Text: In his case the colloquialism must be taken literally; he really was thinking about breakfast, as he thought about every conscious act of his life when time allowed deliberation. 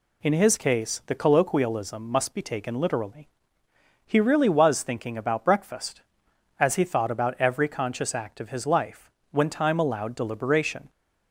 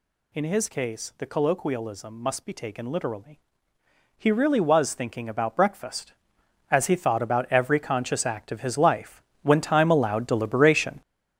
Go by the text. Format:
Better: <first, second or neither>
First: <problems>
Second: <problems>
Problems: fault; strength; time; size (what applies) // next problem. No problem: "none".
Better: first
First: pauses between "life" and "when"; slight; at 9.0 s; 0.22 s long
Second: gets louder; strong; throughout; 8.5 dB // pauses between "life" and "when"; slight; at 9.2 s; 0.22 s long